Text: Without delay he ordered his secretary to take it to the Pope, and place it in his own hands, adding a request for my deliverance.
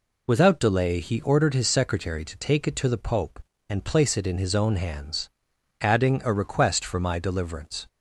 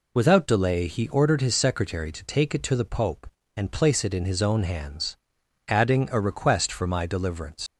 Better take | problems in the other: first | leaves "deliverance" unfinished; at 7.6 s; 80 ms

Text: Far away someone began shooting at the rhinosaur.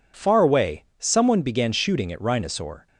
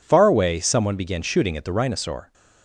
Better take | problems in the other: second | skips "the"; at 2.2 s

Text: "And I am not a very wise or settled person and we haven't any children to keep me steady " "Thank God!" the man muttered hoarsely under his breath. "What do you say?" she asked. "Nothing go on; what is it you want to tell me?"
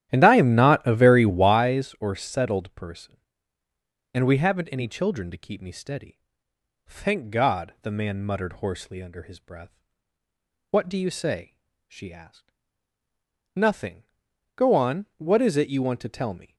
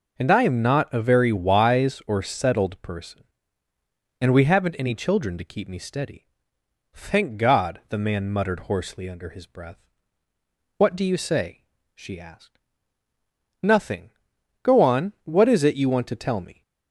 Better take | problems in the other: second | starts louder than the rest; strong; until 1.7 s; 12 dB // pauses between "Nothing" and "go"; noticeable; at 14.0 s; 0.50 s long; noticeable in the second

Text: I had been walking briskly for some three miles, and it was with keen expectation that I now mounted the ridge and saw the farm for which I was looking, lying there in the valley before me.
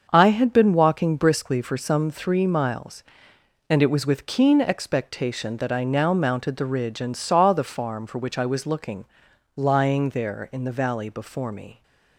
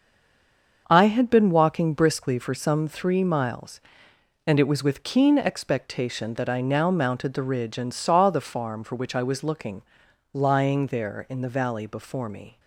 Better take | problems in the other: first | stays silent before the first word; slight; until 0.8 s; 0.8 s long // starts louder than the rest; until 1.8 s; 6.5 dB; also in the first

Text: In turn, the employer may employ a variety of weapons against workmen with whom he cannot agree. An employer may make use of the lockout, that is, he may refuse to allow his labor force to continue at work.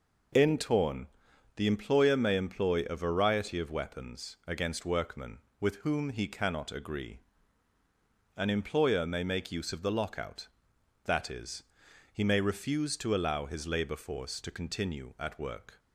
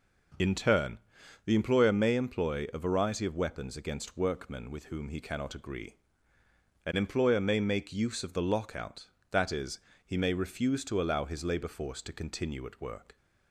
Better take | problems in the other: second | says "torn" for "turn"; at 0.5 s

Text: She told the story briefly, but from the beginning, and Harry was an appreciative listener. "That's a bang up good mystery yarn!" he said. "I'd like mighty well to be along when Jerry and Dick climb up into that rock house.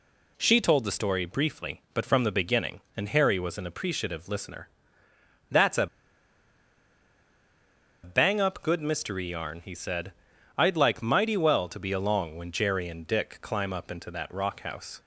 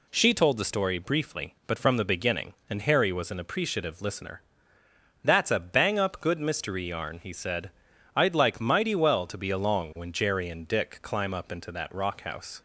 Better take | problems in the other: second | pauses between "a" and "bang"; strong; at 5.8 s; 2.1 s long

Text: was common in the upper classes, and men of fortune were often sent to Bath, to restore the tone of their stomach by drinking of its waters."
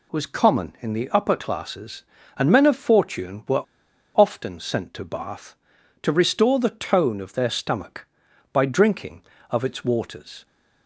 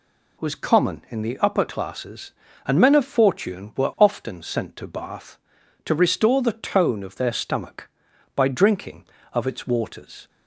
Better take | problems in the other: second | pauses between "were" and "often"; noticeable; at 3.6 s; 0.54 s long

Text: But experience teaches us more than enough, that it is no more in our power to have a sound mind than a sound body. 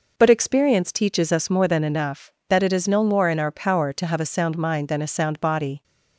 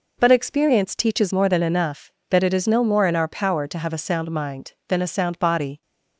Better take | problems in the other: first | skips "us"; at 1.3 s

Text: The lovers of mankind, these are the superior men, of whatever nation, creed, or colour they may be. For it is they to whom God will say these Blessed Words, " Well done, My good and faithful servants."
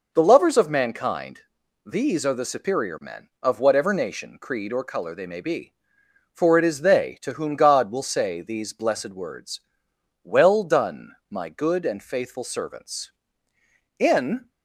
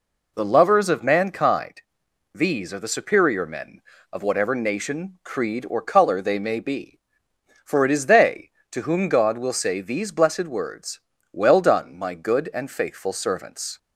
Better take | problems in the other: second | goes on to say "In"; from 13.9 s on; 0.52 s long

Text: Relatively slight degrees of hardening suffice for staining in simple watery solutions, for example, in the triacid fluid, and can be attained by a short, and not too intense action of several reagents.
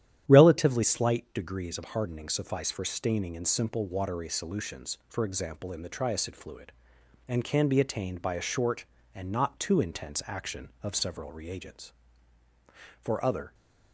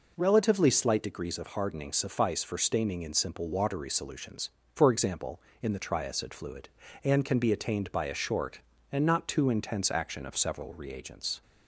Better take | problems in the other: second | starts louder than the rest; strong; until 1.2 s; 11 dB // goes on to say "For other"; from 12.9 s on; 0.54 s long

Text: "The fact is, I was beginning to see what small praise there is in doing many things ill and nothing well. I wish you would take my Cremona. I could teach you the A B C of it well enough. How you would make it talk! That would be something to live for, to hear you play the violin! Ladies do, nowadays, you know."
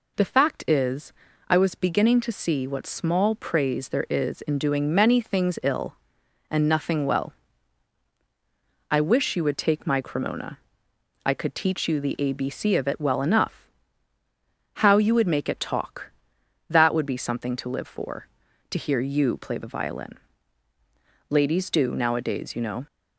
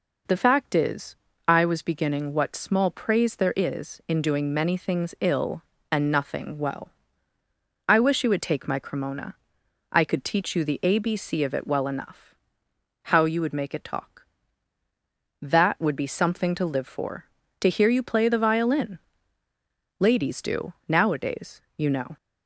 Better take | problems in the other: first | skips "to see"; at 2.3 s

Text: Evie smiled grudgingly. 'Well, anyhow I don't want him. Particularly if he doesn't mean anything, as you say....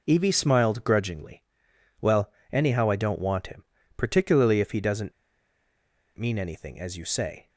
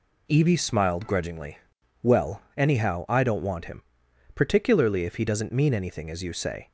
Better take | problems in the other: second | pauses between "doesn't" and "mean"; at 5.1 s; 1.0 s long

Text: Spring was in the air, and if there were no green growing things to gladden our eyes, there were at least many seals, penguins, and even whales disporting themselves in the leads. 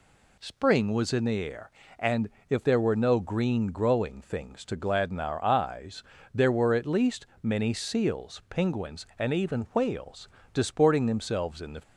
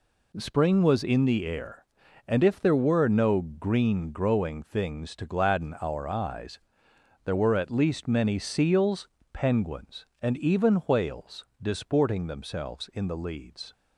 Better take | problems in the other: second | pauses between "and" and "if"; slight; at 2.2 s; 0.18 s long // pauses between "least" and "many"; slight; at 7.2 s; 0.16 s long // pauses between "whales" and "disporting"; slight; at 10.2 s; 0.26 s long; slight in the second // stops before "leads"; at 11.8 s

